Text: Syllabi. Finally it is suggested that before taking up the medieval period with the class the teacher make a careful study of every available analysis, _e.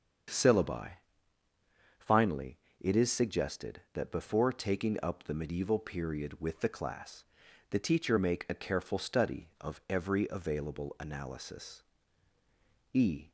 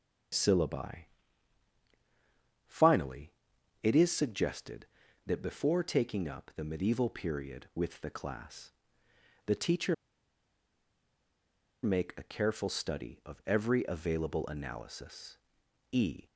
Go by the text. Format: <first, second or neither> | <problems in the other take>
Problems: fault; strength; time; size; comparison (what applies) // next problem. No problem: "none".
first | starts louder than the rest; strong; until 2.9 s; 7.5 dB; also in the first // pauses between "Finally" and "it"; noticeable; at 3.2 s; 0.54 s long; slight in the first // pauses between "class" and "the"; noticeable; at 8.7 s; 0.74 s long; noticeable in the first // pauses between "teacher" and "make"; strong; at 9.9 s; 1.8 s long